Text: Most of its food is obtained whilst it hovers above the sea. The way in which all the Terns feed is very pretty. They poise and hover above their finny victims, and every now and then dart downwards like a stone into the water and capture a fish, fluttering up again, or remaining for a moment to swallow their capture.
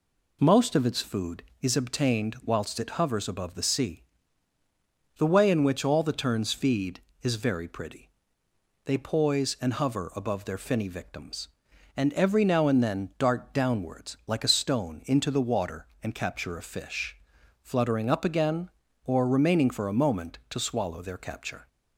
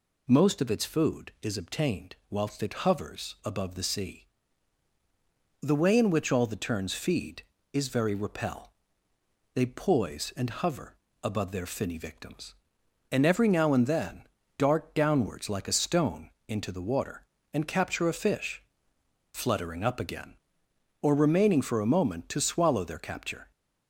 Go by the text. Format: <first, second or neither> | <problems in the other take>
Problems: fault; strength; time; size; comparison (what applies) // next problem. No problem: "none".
first | says "repel" for "pretty"; at 8.1 s // pauses between "hover" and "above"; slight; at 10.9 s; 0.28 s long // pauses between "then" and "dart"; slight; at 14.2 s; 0.34 s long // pauses between "stone" and "into"; slight; at 16.3 s; 0.16 s long